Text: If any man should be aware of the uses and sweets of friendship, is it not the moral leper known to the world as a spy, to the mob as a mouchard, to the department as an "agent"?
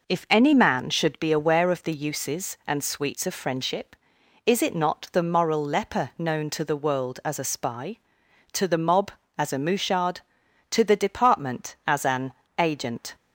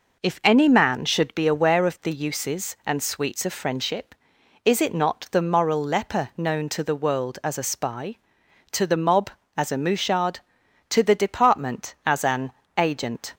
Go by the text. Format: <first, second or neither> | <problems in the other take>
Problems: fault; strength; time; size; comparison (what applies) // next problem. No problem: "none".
neither | pauses between "an" and "agent"; slight; the same in both